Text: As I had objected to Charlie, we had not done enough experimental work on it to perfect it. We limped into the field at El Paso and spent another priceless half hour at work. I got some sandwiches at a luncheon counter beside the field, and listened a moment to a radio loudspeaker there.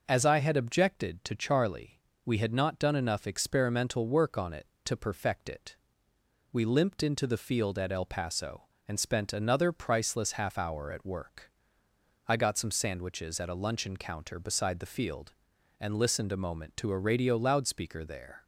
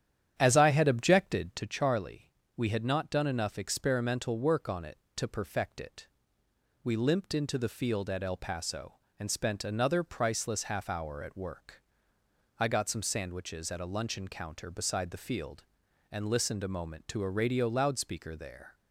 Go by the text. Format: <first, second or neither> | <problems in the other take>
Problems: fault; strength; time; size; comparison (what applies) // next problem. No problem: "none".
first | starts louder than the rest; strong; until 1.6 s; 10 dB